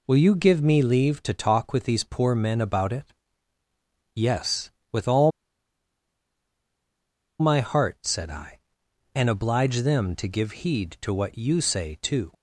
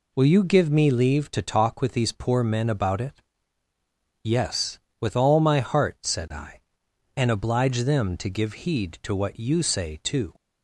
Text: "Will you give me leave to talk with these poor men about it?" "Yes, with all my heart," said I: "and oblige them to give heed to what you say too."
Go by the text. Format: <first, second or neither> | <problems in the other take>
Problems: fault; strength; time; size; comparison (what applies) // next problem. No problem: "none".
second | pauses between "all" and "my"; strong; at 5.3 s; 2.0 s long